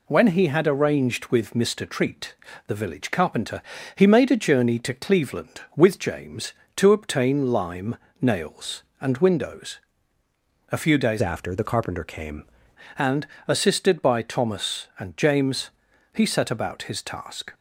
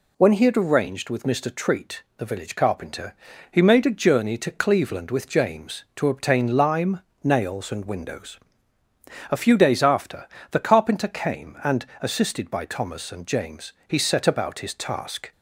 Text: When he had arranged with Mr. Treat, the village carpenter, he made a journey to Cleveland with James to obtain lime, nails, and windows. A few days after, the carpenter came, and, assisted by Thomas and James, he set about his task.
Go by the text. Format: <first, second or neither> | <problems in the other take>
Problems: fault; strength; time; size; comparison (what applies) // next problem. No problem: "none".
second | changes voice from "after" to "came"; from 11.2 to 12.4 s; 1.2 s long